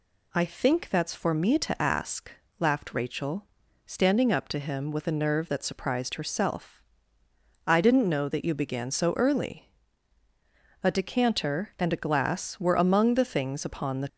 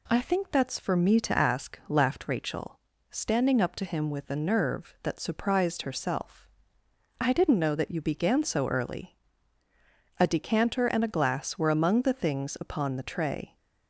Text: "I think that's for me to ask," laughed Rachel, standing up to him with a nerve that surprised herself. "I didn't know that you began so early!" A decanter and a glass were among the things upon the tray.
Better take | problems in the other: second | stops before "tray"; at 14.0 s

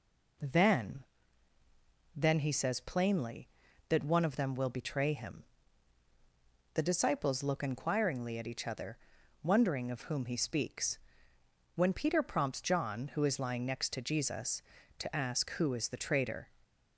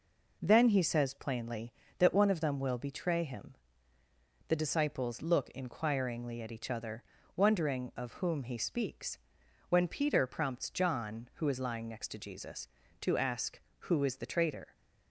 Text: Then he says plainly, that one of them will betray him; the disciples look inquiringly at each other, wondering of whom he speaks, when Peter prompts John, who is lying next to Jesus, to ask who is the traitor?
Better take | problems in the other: second | says "Then" twice; at 2.1 s

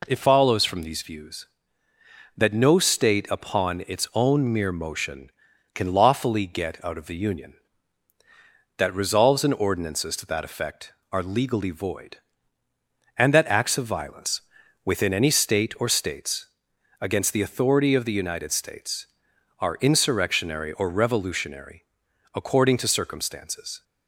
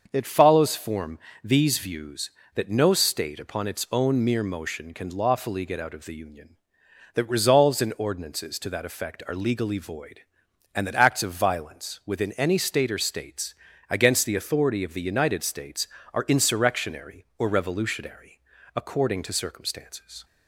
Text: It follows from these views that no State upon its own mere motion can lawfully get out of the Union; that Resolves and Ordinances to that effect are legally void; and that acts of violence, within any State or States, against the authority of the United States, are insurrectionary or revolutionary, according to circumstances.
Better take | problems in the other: first | starts louder than the rest; until 1.1 s; 6.5 dB // says "form" for "from"; at 0.7 s

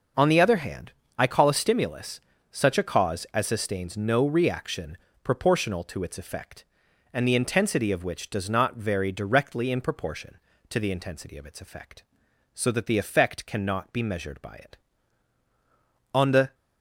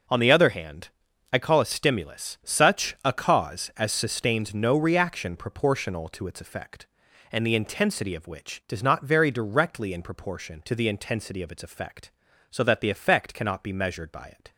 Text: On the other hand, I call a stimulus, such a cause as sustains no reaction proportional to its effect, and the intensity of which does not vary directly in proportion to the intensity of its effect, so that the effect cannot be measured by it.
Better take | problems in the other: second | pauses between "reaction" and "proportional"; slight; at 4.9 s; 0.26 s long // goes on to say "On the"; slight; from 16.1 s on; 0.42 s long

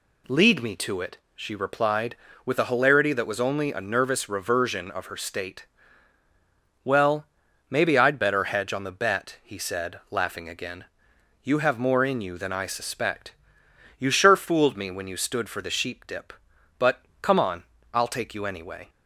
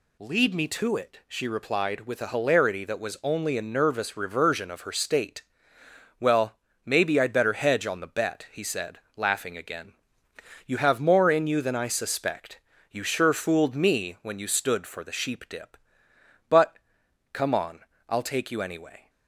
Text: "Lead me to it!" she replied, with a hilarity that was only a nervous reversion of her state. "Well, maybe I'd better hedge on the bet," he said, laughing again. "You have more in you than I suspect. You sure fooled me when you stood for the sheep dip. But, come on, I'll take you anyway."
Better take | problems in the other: neither | none

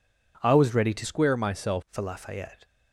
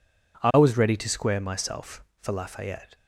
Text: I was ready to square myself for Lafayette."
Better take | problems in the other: second | changes voice from "square" to "myself"; from 1.0 to 1.8 s; 0.8 s long

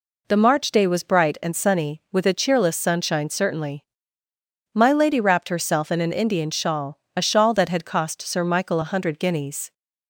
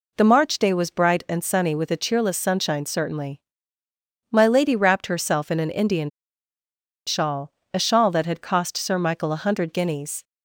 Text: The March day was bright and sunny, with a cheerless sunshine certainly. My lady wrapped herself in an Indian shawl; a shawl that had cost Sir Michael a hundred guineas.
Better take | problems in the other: first | pauses between "Indian" and "shawl"; noticeable; at 6.1 s; 0.97 s long

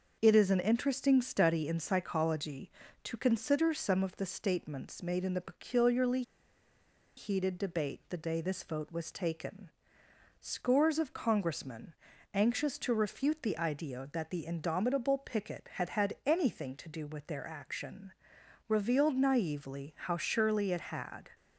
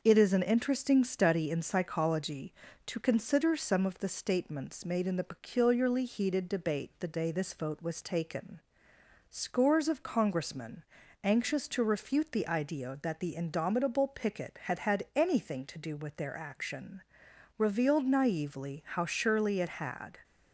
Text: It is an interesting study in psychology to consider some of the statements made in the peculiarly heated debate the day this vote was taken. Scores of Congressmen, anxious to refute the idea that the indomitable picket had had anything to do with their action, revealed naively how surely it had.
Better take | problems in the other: second | starts louder than the rest; noticeable; until 1.2 s; 6 dB; noticeable in the second // pauses between "peculiarly" and "heated"; noticeable; at 6.2 s; 0.94 s long

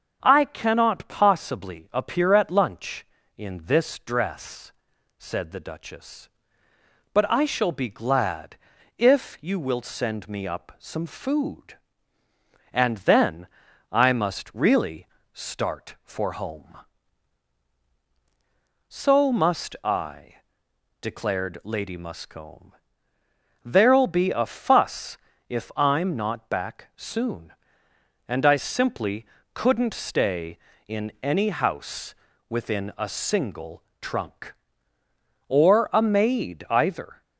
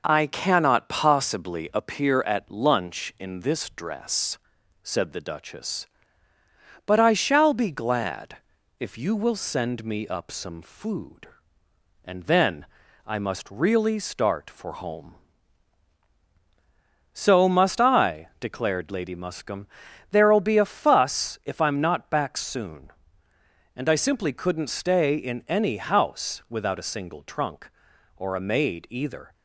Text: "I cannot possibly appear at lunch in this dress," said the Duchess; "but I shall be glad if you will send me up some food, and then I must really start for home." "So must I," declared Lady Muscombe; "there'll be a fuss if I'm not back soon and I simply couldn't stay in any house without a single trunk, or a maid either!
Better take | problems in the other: second | starts louder than the rest; until 1.2 s; 6.5 dB // pauses between "glad" and "if"; at 8.5 s; 0.42 s long; also in the second // pauses between "then" and "I"; at 13.4 s; 0.44 s long; also in the second // pauses between "really" and "start"; slight; at 15.0 s; 0.26 s long // pauses between "fuss" and "if"; slight; at 25.1 s; 0.32 s long // pauses between "simply" and "couldn't"; slight; at 29.2 s; 0.28 s long // says "within" for "without"; at 32.4 s // pauses between "single" and "trunk"; slight; at 33.8 s; 0.18 s long

